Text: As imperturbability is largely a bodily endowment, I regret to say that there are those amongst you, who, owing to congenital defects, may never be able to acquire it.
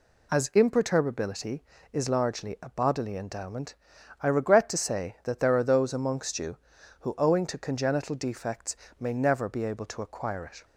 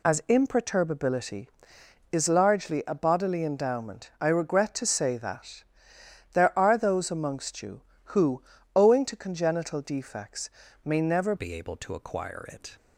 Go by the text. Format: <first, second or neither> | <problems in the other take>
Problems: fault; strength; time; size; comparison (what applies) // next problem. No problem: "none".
first | pauses between "that" and "there"; noticeable; at 5.6 s; 0.70 s long // changes voice at "be"; from 11.3 s on; 1.4 s long